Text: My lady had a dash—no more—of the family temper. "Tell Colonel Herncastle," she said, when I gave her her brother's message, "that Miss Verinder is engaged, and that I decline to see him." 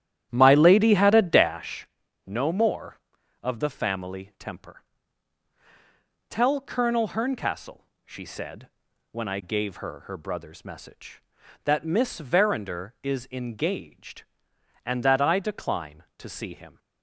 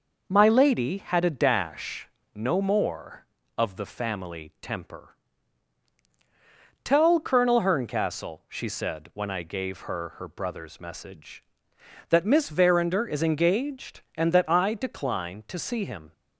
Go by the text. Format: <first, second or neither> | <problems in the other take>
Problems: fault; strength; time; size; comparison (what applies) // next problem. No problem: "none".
second | starts louder than the rest; strong; until 1.6 s; 11 dB